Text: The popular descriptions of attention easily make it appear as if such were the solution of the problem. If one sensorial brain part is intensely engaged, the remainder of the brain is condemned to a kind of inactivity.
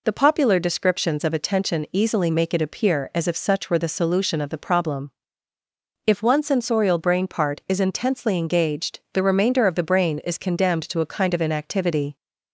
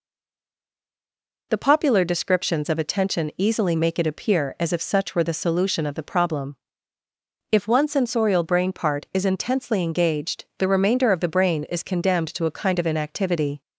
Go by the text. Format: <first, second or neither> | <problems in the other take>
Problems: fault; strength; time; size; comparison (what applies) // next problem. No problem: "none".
first | stays silent before the first word; noticeable; until 1.5 s; 1.5 s long